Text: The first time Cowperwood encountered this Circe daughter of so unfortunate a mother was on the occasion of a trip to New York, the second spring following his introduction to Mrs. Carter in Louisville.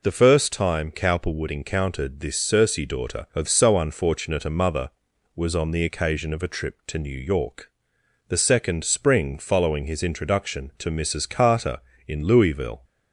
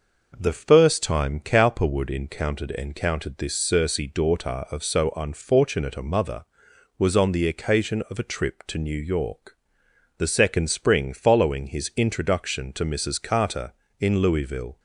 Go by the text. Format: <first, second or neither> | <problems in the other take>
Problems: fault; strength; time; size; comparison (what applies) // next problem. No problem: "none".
first | says "encountered" twice; at 2.7 s